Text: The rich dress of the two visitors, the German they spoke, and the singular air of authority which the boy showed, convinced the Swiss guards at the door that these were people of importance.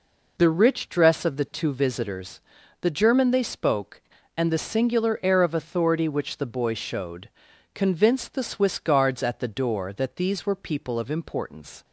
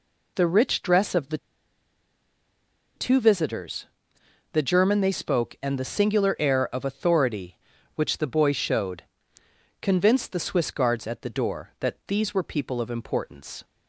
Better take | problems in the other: first | pauses between "the" and "two"; strong; at 1.3 s; 1.5 s long

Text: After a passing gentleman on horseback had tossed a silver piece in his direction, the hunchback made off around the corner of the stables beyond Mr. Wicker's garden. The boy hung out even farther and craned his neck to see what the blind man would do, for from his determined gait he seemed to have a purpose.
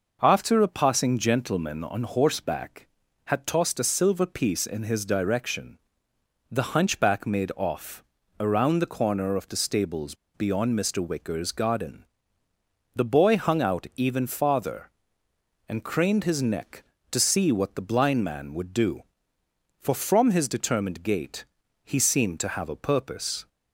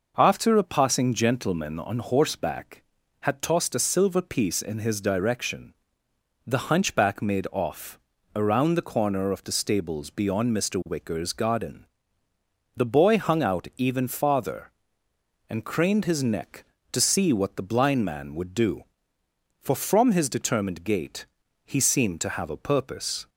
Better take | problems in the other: second | pauses between "off" and "around"; slight; at 8.0 s; 0.34 s long; slight in the second // pauses between "stables" and "beyond"; slight; at 10.1 s; 0.20 s long // pauses between "gait" and "he"; at 21.4 s; 0.38 s long; also in the second

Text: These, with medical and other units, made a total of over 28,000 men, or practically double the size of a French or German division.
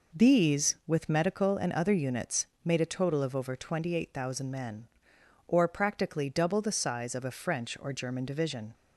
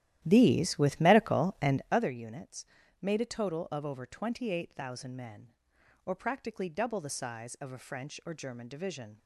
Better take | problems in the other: first | starts louder than the rest; strong; until 2.1 s; 13 dB

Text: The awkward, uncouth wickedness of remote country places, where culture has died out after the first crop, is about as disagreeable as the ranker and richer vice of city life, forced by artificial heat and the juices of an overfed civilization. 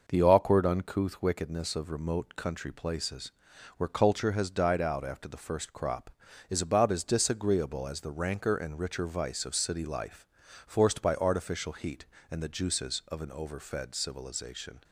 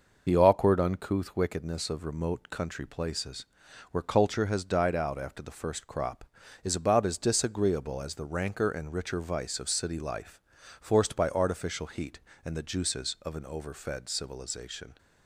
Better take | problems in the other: first | loses the start of "The"; at 0.2 s; 40 ms

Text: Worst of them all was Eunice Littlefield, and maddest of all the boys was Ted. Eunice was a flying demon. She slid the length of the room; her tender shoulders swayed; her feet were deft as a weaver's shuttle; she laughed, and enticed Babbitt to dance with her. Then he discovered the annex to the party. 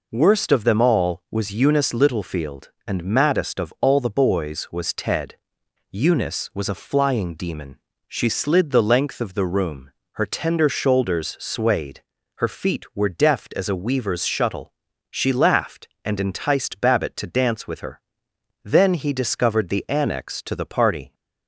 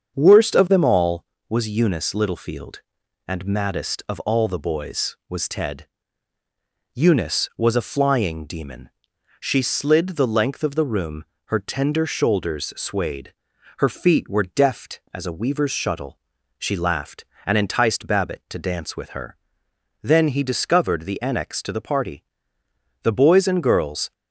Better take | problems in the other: first | starts louder than the rest; until 1.1 s; 7 dB // goes on to say "The boys and girls"; noticeable; from 23.0 s on; 1.1 s long

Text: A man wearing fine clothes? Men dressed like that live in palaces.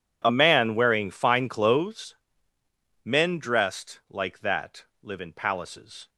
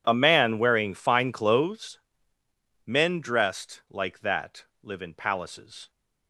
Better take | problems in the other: neither | pauses between "that" and "live"; slight; the same in both

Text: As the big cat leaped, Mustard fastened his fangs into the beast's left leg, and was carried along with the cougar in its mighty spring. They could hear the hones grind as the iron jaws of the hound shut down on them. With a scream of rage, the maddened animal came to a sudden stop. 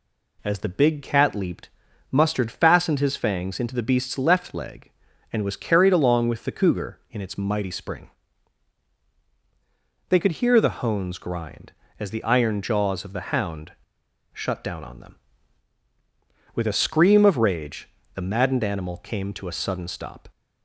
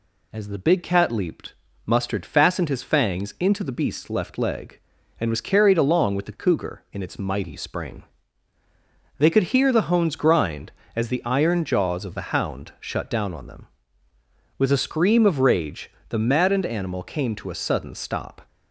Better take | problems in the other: second | pauses between "hound" and "shut"; noticeable; at 13.7 s; 0.62 s long

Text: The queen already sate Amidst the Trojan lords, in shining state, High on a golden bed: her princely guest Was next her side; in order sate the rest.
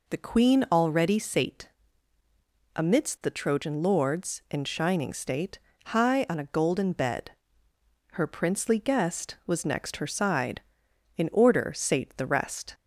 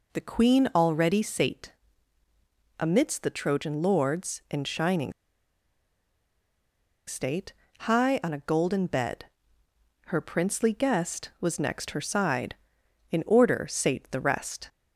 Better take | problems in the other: first | pauses between "sate" and "Amidst"; at 1.7 s; 1.0 s long; also in the first // pauses between "shining" and "state"; strong; at 5.1 s; 1.9 s long

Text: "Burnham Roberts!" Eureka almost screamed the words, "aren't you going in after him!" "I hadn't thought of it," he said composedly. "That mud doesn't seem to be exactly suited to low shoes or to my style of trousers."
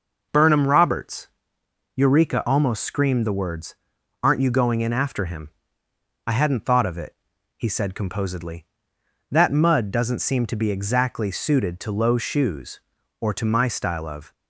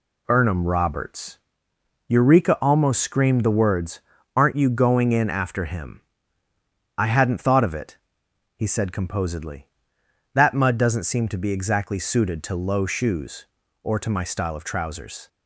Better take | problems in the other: second | stops before "trousers"; at 14.3 s

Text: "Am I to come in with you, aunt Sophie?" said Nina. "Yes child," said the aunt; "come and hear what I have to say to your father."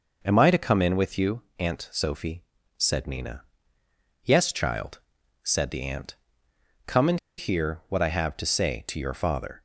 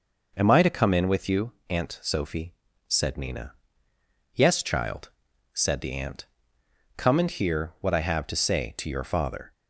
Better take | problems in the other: second | pauses between "and" and "hear"; slight; at 7.1 s; 0.19 s long

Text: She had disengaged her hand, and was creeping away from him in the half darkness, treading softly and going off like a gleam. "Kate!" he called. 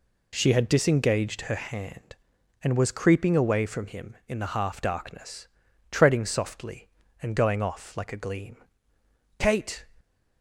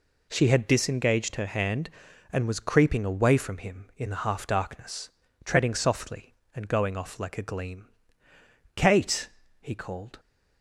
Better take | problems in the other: second | stops before "he called"; at 9.9 s

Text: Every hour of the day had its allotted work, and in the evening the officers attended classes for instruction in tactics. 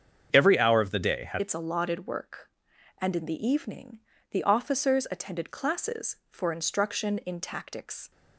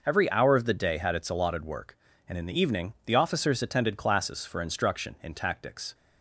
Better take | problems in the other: second | starts louder than the rest; strong; until 1.3 s; 7.5 dB // changes voice at "its"; from 1.4 s on; 6.7 s long // pauses between "evening" and "the"; slight; at 3.9 s; 0.32 s long

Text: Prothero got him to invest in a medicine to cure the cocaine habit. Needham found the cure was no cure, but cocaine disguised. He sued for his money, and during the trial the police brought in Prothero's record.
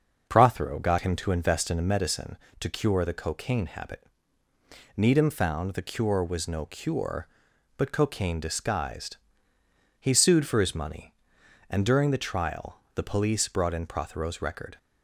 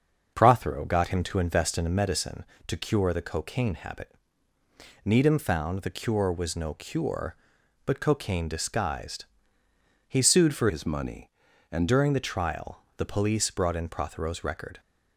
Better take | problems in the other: first | starts louder than the rest; until 1.3 s; 6.5 dB; also in the first // changes voice from "his" to "and"; from 10.6 to 11.8 s; 1.2 s long

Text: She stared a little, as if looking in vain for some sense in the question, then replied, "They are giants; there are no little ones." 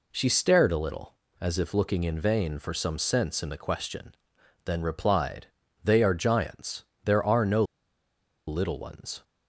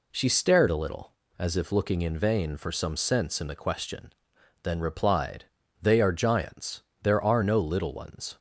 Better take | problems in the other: second | pauses between "no" and "little"; noticeable; at 7.6 s; 0.83 s long

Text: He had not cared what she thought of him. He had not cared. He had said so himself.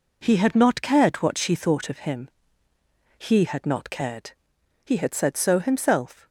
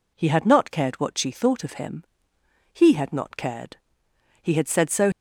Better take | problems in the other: first | stops before "himself"; at 5.1 s

